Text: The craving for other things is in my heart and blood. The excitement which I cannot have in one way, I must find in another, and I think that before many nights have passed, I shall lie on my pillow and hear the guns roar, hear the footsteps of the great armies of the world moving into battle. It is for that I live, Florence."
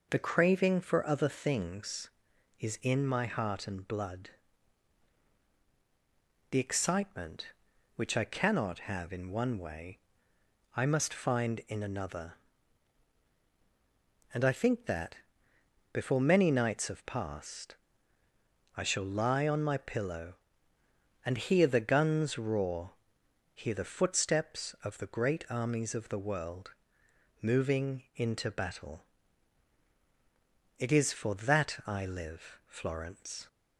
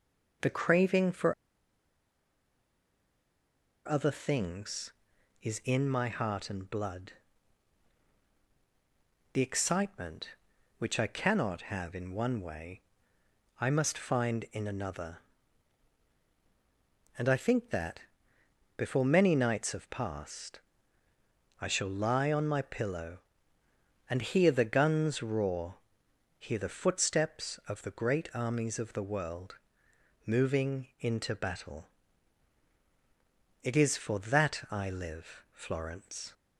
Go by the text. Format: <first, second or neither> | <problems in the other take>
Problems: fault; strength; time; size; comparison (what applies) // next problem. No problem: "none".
first | pauses between "for" and "other"; strong; at 1.3 s; 2.5 s long // pauses between "that" and "before"; noticeable; at 17.9 s; 0.76 s long; noticeable in the first // pauses between "world" and "moving"; noticeable; at 29.5 s; 0.70 s long; noticeable in the first